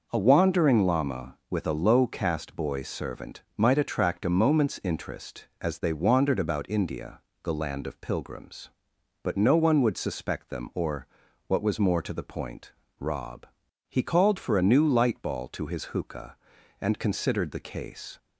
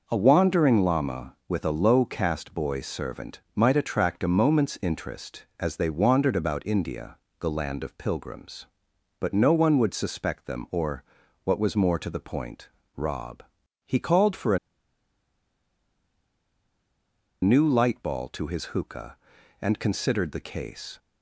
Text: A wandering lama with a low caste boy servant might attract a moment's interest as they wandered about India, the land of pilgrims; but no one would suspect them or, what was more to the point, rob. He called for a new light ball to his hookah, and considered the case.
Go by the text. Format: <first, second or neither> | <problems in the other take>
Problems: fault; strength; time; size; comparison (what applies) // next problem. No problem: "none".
first | pauses between "servant" and "might"; slight; at 3.4 s; 0.16 s long; slight in the first // pauses between "a" and "new"; strong; at 14.5 s; 2.8 s long